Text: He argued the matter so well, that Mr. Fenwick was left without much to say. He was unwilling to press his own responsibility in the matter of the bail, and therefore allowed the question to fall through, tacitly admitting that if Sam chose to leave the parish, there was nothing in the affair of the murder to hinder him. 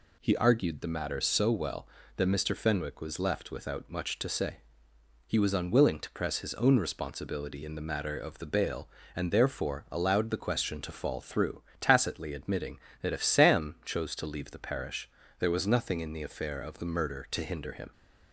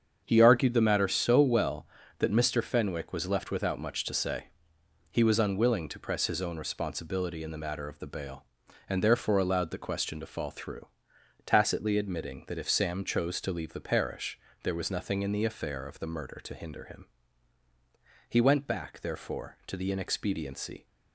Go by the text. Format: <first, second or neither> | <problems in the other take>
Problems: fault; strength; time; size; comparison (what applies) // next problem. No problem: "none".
first | starts louder than the rest; strong; until 1.2 s; 7.5 dB // goes on to say "He went back therefore to the inexpediency"; strong; from 18.2 s on; 2.5 s long